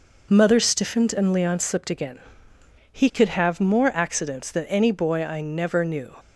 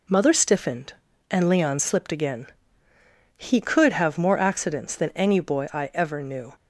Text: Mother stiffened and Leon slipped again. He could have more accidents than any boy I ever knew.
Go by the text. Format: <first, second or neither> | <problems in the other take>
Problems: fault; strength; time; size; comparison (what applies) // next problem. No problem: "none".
second | says "never" for "ever"; at 5.4 s